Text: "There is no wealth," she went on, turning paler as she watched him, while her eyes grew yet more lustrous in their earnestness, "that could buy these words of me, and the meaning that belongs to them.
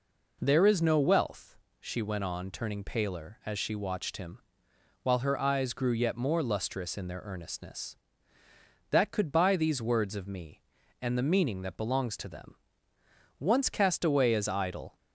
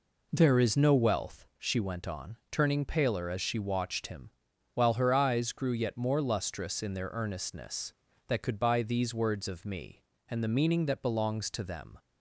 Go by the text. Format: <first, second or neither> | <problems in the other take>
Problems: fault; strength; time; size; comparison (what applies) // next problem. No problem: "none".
second | goes on to say "Once cast away as idle"; from 13.3 s on; 1.5 s long